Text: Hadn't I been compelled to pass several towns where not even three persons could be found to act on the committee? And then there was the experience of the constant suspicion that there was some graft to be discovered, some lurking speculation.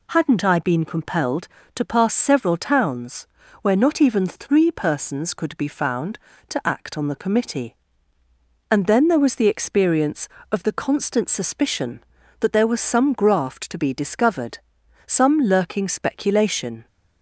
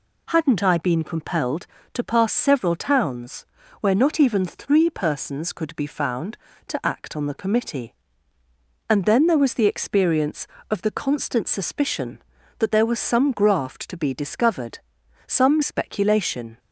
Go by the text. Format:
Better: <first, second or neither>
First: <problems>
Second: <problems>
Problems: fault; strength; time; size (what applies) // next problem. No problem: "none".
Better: first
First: pauses between "towns" and "where"; slight; at 3.2 s; 0.36 s long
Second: pauses between "towns" and "where"; slight; at 3.4 s; 0.36 s long // skips "lurking"; at 15.6 s